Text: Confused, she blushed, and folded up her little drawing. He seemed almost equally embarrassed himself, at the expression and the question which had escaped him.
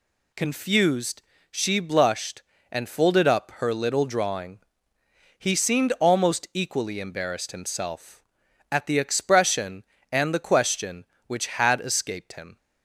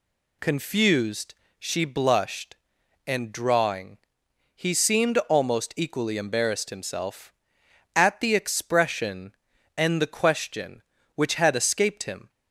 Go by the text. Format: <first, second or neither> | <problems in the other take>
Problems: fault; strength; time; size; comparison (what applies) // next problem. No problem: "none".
first | skips "folded up her little"; at 3.3 s